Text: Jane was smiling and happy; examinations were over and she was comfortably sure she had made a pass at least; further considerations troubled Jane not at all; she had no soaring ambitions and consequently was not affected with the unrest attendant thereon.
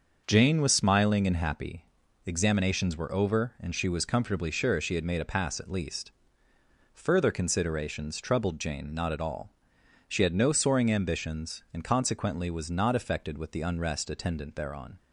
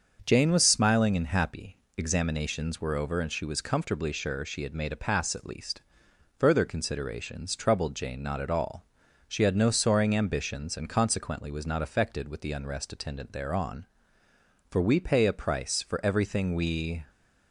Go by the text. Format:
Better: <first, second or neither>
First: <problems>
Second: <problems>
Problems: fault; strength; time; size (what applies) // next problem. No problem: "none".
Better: first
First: starts louder than the rest; until 1.2 s; 6.5 dB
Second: starts louder than the rest; until 1.2 s; 6.5 dB // goes on to say "For we pay a price for everything we"; strong; from 14.6 s on; 2.3 s long